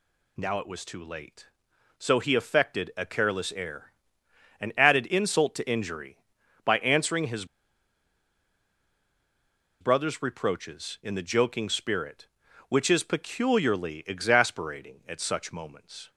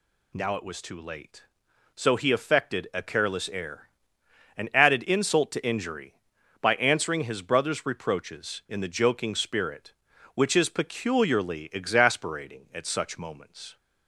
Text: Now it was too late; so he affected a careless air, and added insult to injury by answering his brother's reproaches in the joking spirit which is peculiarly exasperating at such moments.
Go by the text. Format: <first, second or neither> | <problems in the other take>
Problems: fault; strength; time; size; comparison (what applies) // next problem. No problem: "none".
second | pauses between "his" and "brother's"; strong; at 7.4 s; 2.3 s long